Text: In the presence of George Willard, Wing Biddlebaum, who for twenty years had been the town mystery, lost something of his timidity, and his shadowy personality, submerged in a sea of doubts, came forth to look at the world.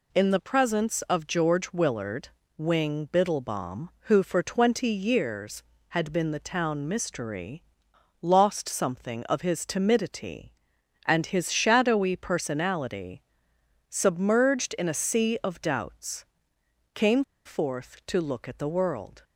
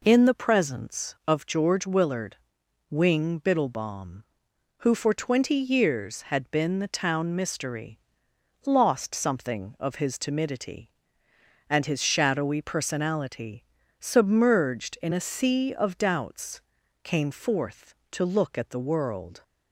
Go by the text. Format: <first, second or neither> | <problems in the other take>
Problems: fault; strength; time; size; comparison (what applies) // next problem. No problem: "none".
second | pauses between "came" and "forth"; slight; at 17.2 s; 0.23 s long